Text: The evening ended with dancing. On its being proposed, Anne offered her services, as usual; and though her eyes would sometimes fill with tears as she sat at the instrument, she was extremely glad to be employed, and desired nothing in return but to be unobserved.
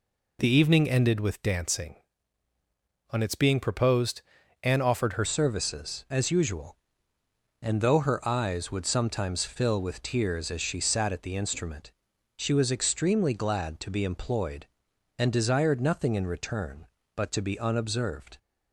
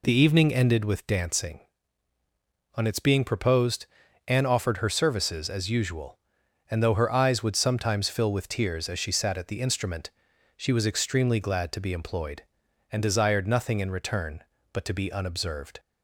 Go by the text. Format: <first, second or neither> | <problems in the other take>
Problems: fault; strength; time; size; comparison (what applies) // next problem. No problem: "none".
second | changes voice at "services"; from 5.2 s on; 13.1 s long